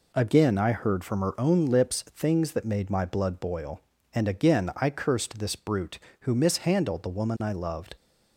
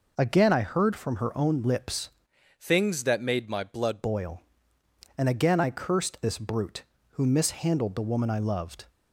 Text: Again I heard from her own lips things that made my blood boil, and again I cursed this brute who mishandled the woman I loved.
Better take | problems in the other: first | changes voice from "things" to "blood"; from 2.6 to 4.0 s; 1.4 s long

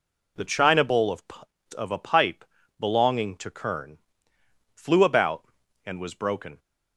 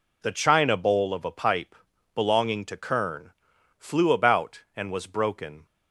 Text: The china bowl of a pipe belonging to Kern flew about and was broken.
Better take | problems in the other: second | says "of" twice; at 1.7 s // pauses between "pipe" and "belonging"; slight; at 2.4 s; 0.34 s long; also in the second // pauses between "Kern" and "flew"; noticeable; at 3.9 s; 0.78 s long; noticeable in the second

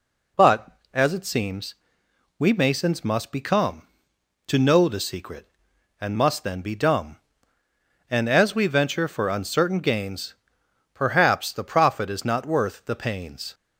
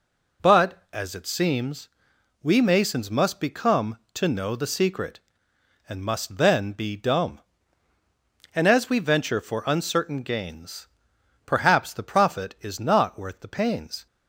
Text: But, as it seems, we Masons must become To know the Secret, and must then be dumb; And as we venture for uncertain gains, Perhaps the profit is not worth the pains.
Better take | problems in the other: neither | none

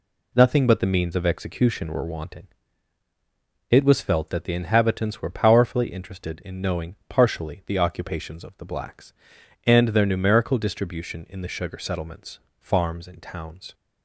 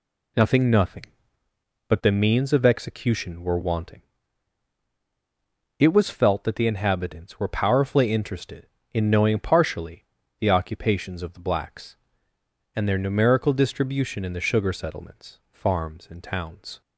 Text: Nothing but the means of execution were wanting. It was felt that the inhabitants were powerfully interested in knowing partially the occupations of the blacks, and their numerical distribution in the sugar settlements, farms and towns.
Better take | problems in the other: first | says "Nothing" twice; at 0.6 s // pauses between "partially" and "the"; slight; at 10.0 s; 0.34 s long

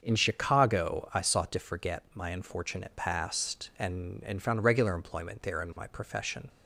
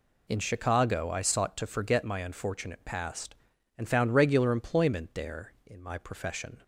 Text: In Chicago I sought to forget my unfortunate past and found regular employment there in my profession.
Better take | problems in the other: second | starts louder than the rest; until 1.0 s; 6.5 dB // says "and" twice; at 4.2 s

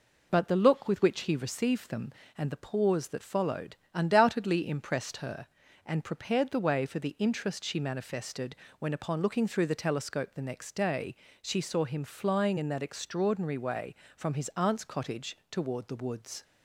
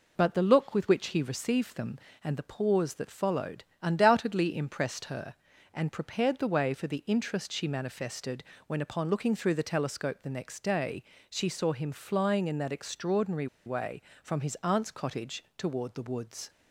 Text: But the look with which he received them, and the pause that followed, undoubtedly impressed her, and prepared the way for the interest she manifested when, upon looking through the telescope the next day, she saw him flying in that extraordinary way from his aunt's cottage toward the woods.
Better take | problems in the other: first | pauses between "manifested" and "when"; slight; at 8.4 s; 0.24 s long; slight in the first // pauses between "extraordinary" and "way"; slight; at 13.4 s; 0.19 s long

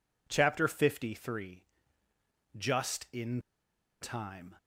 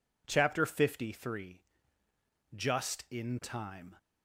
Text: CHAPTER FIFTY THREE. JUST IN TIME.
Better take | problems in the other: second | pauses between "IN" and "TIME"; noticeable; at 3.4 s; 0.60 s long

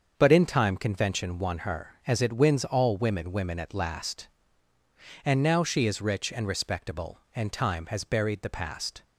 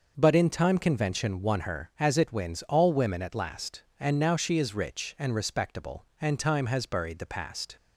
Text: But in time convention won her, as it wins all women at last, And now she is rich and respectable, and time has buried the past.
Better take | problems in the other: second | starts louder than the rest; until 1.1 s; 7 dB // says "women" twice; at 3.3 s

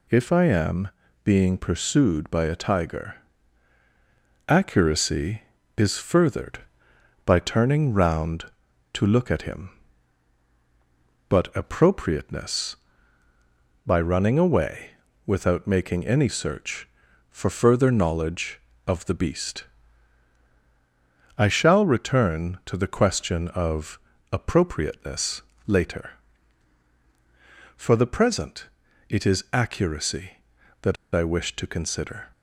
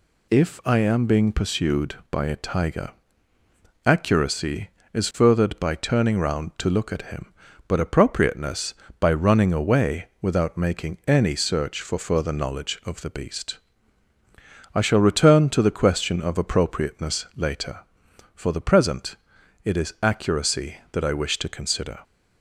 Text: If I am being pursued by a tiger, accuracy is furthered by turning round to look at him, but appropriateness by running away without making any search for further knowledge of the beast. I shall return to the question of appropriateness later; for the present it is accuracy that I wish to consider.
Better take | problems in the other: second | pauses between "am" and "being"; at 0.8 s; 0.38 s long // pauses between "away" and "without"; slight; at 14.9 s; 0.34 s long; slight in the second // pauses between "of" and "appropriateness"; slight; at 23.9 s; 0.32 s long // pauses between "appropriateness" and "later"; slight; at 25.4 s; 0.24 s long // pauses between "present" and "it"; at 28.6 s; 0.42 s long; noticeable in the second // pauses between "that" and "I"; slight; at 30.9 s; 0.18 s long

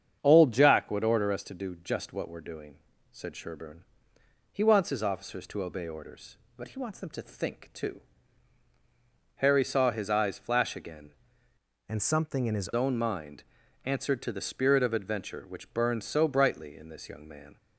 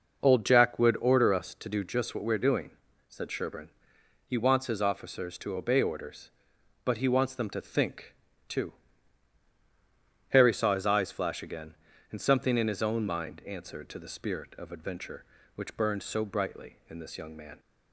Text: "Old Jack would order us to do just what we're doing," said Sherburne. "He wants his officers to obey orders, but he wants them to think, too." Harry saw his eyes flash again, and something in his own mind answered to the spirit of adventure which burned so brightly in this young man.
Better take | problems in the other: second | starts louder than the rest; strong; until 1.2 s; 7.5 dB // changes voice from "and" to "his"; from 11.8 to 12.7 s; 0.9 s long // pauses between "mind" and "answered"; at 13.4 s; 0.42 s long

